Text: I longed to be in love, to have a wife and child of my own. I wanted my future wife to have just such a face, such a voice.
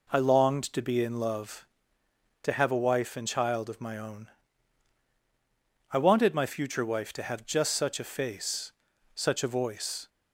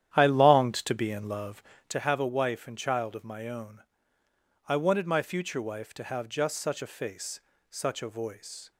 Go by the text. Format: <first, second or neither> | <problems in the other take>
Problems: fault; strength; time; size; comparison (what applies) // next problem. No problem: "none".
first | starts louder than the rest; strong; until 1.9 s; 10.5 dB